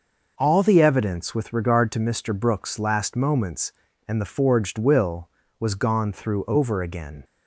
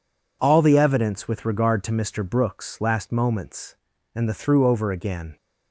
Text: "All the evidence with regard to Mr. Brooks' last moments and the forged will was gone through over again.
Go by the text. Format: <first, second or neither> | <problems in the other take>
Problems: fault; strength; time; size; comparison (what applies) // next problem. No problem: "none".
first | skips "forged will was gone"; at 4.3 s